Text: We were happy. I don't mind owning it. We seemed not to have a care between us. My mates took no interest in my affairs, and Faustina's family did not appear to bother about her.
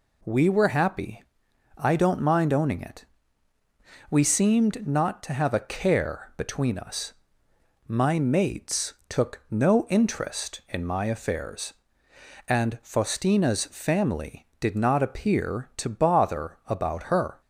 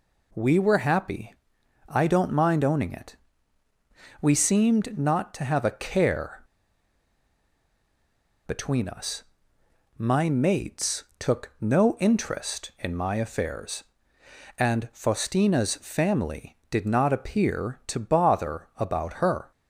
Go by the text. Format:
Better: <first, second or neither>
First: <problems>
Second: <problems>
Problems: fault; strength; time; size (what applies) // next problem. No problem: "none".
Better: first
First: pauses between "mates" and "took"; slight; at 8.9 s; 0.16 s long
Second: pauses between "care" and "between"; strong; at 6.4 s; 2.0 s long // pauses between "mates" and "took"; slight; at 11.0 s; 0.16 s long